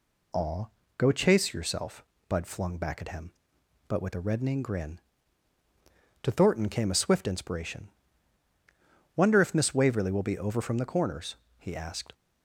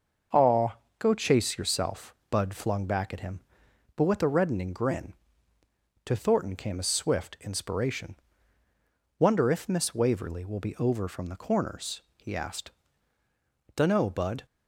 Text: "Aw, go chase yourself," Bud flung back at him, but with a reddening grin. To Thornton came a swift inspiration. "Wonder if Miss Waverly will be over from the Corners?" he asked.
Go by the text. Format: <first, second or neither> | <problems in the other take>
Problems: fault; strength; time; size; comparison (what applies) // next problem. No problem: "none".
first | starts louder than the rest; until 1.5 s; 6.5 dB // goes on to say "Dunno Bud"; noticeable; from 13.7 s on; 0.70 s long